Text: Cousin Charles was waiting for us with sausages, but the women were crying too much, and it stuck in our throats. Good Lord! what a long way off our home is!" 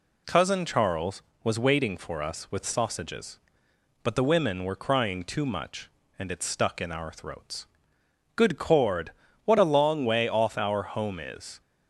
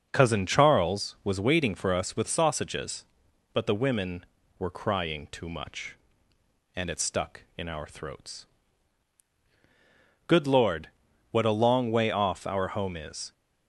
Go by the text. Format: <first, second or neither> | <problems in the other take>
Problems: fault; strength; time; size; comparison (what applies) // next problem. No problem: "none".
second | says "Cord" for "Lord"; at 8.5 s